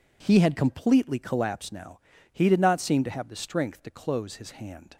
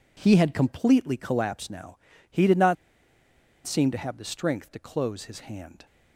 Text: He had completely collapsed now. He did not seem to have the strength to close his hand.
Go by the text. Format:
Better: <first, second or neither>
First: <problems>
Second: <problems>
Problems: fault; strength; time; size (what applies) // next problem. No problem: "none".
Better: first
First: none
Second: pauses between "not" and "seem"; noticeable; at 2.7 s; 0.89 s long